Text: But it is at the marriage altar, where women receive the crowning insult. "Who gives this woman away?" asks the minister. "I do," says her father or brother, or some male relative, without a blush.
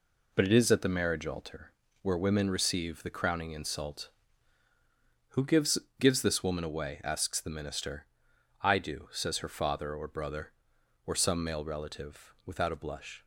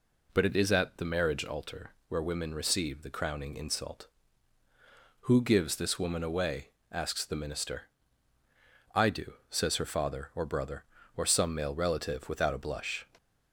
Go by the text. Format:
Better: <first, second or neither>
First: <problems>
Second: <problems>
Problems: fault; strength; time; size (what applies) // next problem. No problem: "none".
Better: second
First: says "gives" twice; at 6.0 s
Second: none